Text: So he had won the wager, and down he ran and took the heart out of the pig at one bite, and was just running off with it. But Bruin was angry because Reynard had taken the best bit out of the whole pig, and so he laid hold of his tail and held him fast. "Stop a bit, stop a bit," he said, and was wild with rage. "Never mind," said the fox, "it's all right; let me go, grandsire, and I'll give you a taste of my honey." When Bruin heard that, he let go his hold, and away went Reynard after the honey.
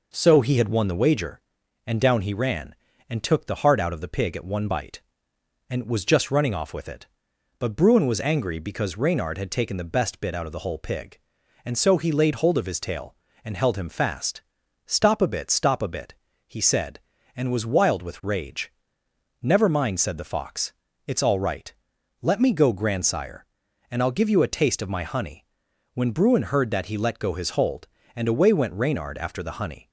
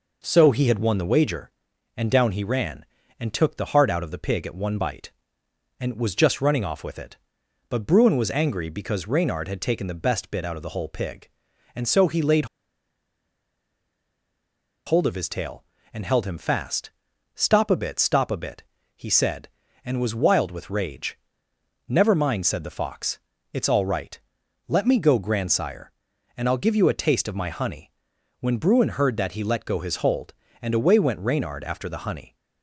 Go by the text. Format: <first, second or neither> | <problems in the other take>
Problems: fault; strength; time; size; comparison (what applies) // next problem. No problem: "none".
first | pauses between "laid" and "hold"; strong; at 12.4 s; 2.3 s long